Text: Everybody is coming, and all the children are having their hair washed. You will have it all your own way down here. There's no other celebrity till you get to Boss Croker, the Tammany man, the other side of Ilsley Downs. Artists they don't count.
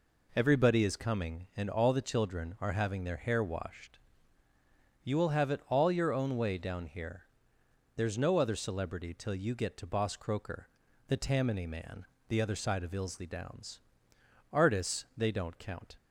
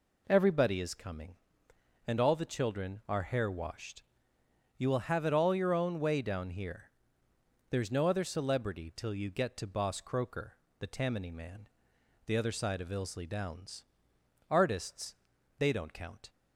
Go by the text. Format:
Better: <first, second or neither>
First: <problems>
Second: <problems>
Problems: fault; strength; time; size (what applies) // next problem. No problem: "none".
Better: first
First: none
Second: skips "having their"; at 3.2 s // pauses between "Artists" and "they"; at 15.1 s; 0.44 s long